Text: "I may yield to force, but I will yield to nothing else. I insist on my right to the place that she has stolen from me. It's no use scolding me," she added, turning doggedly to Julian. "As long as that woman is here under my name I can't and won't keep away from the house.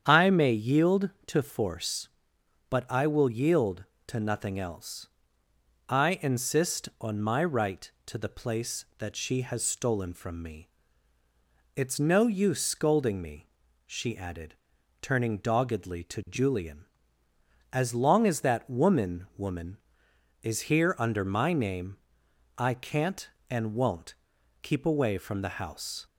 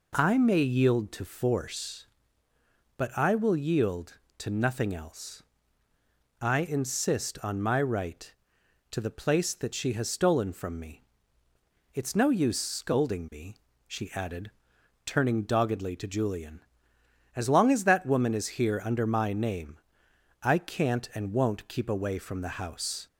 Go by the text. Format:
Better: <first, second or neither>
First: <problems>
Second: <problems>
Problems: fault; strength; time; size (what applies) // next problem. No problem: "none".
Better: second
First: starts louder than the rest; strong; until 1.0 s; 8.5 dB // says "woman" twice; at 19.3 s // pauses between "name" and "I"; noticeable; at 21.9 s; 0.62 s long // pauses between "won't" and "keep"; noticeable; at 24.1 s; 0.48 s long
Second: pauses between "name" and "I"; noticeable; at 19.7 s; 0.64 s long